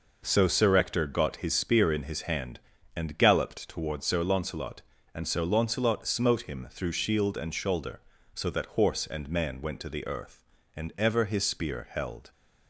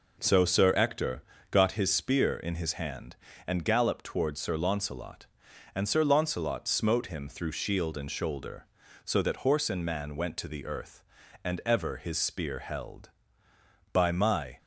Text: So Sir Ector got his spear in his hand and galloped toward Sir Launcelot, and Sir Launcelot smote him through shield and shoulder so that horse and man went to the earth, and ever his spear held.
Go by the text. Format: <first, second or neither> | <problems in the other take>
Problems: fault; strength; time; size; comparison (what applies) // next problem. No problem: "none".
first | pauses between "Ector" and "got"; slight; at 1.2 s; 0.28 s long // goes on to say "By my"; noticeable; from 13.9 s on; 0.66 s long